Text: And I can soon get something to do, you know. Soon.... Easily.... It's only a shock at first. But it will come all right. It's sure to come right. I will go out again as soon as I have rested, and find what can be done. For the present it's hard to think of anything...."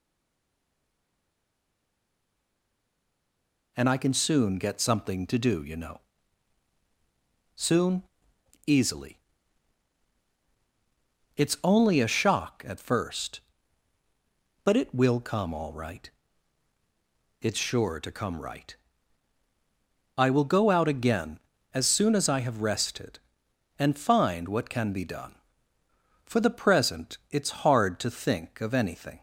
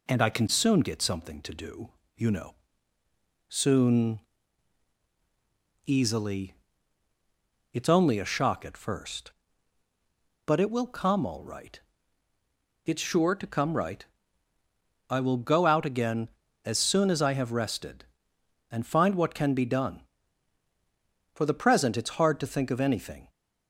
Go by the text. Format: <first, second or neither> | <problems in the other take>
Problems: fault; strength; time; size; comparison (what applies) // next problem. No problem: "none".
second | stays silent before the first word; strong; until 3.7 s; 3.7 s long